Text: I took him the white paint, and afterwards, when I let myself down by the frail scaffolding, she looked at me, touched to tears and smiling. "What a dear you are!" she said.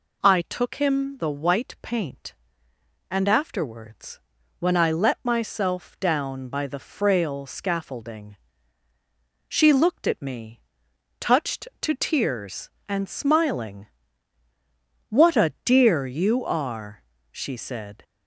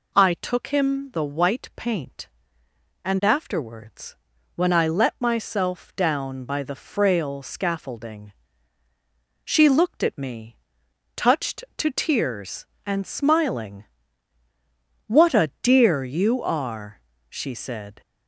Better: neither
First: none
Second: none

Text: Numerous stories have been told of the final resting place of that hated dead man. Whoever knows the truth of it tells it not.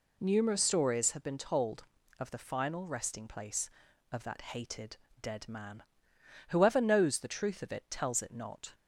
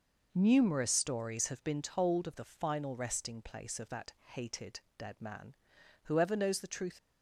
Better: first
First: pauses between "hated" and "dead"; slight; at 4.9 s; 0.26 s long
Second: pauses between "hated" and "dead"; slight; at 4.8 s; 0.18 s long // stops before "of it tells it not"; at 6.9 s

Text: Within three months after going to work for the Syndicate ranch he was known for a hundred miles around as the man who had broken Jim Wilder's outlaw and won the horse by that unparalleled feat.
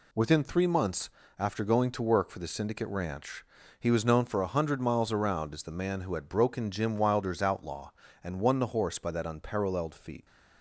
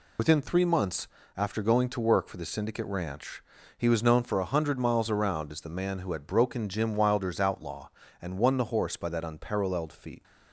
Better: first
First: pauses between "months" and "after"; slight; at 1.0 s; 0.30 s long // pauses between "ranch" and "he"; slight; at 3.4 s; 0.34 s long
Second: loses the start of "Within"; at 0.1 s; 85 ms // pauses between "months" and "after"; slight; at 1.0 s; 0.30 s long // pauses between "ranch" and "he"; slight; at 3.4 s; 0.34 s long

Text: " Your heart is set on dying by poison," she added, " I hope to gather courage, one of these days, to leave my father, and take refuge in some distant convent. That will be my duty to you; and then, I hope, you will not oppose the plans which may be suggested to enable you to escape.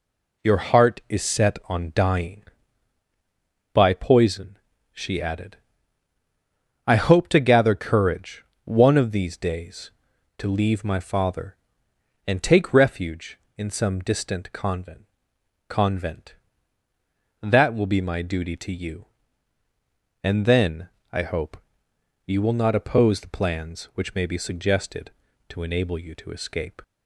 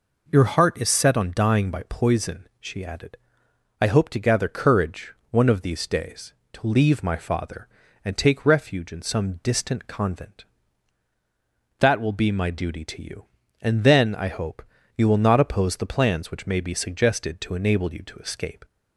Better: second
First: says "convent" twice; at 15.6 s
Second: none

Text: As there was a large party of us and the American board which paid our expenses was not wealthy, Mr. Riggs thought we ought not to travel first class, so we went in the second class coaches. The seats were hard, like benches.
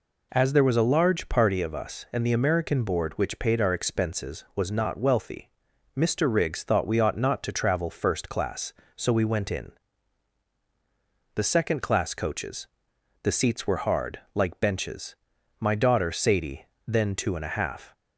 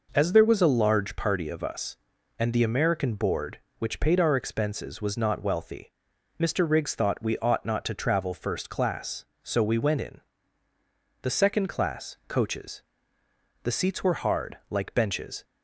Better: second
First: pauses between "in" and "the"; strong; at 9.7 s; 1.6 s long // goes on to say "My daughter Sadie then two and a half"; strong; from 15.5 s on; 2.3 s long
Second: pauses between "in" and "the"; at 10.1 s; 1.0 s long

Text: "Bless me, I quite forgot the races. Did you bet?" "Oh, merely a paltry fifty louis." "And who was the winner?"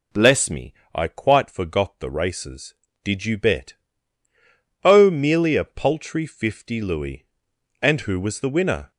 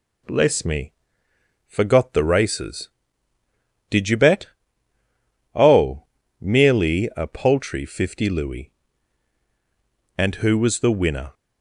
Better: first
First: none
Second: skips "I quite"; at 1.3 s

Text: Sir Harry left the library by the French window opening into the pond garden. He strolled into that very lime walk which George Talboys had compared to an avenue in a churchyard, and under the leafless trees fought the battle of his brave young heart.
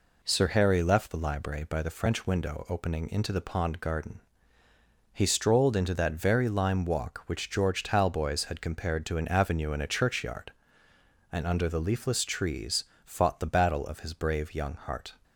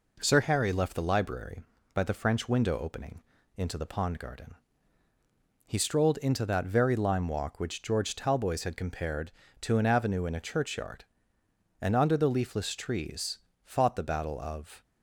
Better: first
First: pauses between "trees" and "fought"; slight; at 12.8 s; 0.20 s long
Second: pauses between "opening" and "into"; slight; at 3.2 s; 0.34 s long // pauses between "trees" and "fought"; slight; at 13.3 s; 0.26 s long // stops before "his brave young heart"; at 14.8 s

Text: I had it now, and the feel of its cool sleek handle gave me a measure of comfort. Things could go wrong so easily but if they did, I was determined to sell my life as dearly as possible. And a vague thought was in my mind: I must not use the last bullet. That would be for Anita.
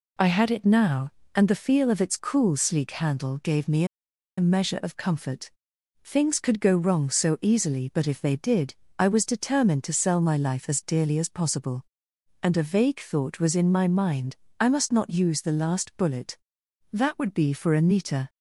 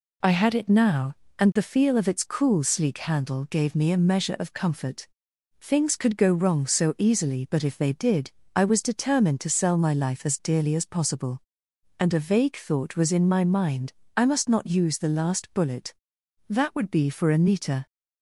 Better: second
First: pauses between "me" and "a"; noticeable; at 3.8 s; 0.52 s long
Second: none

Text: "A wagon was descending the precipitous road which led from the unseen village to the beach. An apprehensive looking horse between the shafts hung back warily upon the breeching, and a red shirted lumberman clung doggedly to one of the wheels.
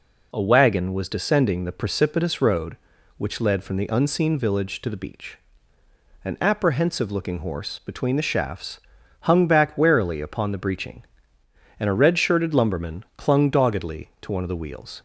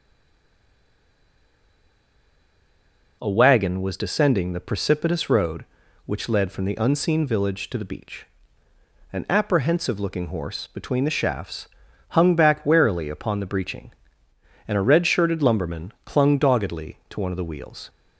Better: first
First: pauses between "shafts" and "hung"; at 8.7 s; 0.42 s long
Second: stays silent before the first word; strong; until 3.2 s; 3.2 s long // pauses between "shafts" and "hung"; at 11.6 s; 0.42 s long

